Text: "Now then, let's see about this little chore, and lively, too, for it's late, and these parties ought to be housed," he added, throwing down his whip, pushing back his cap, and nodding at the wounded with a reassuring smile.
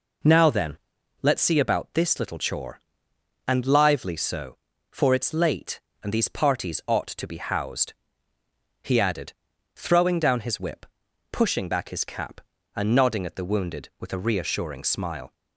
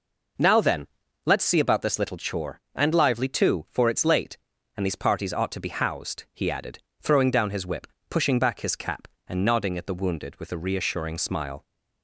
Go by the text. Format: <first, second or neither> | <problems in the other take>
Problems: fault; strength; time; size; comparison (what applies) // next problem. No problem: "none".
second | says "so" for "too"; at 4.1 s